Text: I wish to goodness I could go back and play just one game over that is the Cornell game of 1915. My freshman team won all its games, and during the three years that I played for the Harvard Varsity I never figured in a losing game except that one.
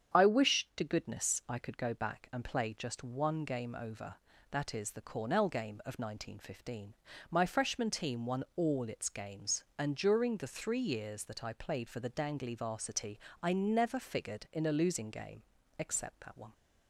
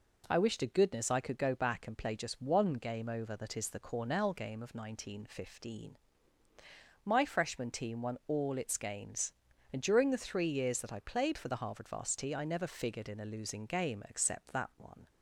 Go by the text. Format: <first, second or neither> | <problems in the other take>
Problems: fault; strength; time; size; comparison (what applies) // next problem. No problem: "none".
second | starts louder than the rest; strong; until 1.2 s; 8 dB // says "Dangly" for "Harvard"; at 12.1 s // pauses between "Varsity" and "I"; slight; at 13.1 s; 0.24 s long // pauses between "game" and "except"; at 15.4 s; 0.38 s long